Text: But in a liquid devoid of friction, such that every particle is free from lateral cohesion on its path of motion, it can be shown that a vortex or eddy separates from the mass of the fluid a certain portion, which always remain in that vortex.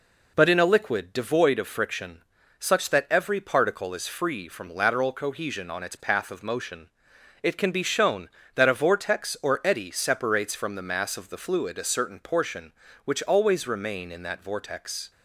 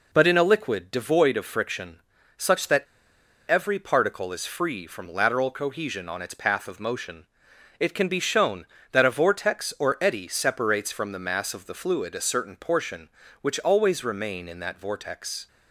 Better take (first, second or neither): first